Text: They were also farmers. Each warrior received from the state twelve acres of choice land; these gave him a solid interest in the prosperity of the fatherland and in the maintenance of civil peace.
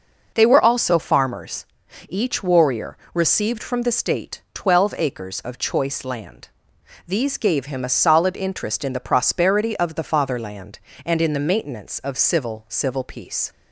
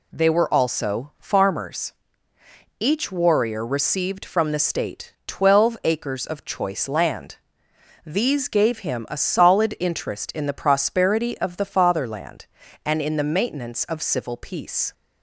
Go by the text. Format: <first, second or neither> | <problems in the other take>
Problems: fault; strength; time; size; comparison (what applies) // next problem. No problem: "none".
second | pauses between "warrior" and "received"; slight; at 2.9 s; 0.16 s long // says "civil" twice; at 12.6 s